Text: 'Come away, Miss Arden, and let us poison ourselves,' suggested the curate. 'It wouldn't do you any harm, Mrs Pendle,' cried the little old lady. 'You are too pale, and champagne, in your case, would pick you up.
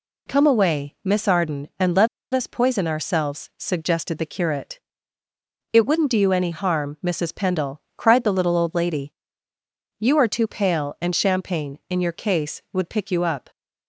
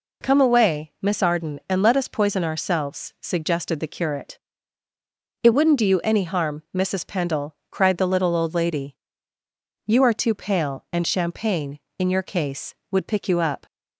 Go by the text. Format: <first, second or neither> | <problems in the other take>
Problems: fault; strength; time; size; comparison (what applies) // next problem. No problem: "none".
second | pauses between "let" and "us"; slight; at 2.0 s; 0.26 s long